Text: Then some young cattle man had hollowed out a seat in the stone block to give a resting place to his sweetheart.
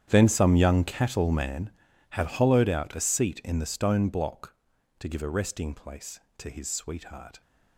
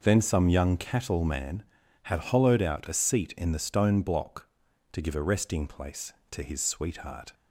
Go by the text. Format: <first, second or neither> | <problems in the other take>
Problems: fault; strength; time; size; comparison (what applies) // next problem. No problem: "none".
second | gets quieter; strong; throughout; 18 dB